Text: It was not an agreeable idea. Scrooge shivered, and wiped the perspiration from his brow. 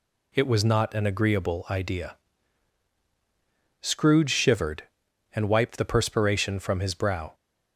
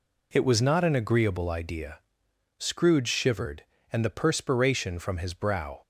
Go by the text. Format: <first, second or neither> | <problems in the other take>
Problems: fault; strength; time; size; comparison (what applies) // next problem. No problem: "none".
first | skips "wiped"; at 4.0 s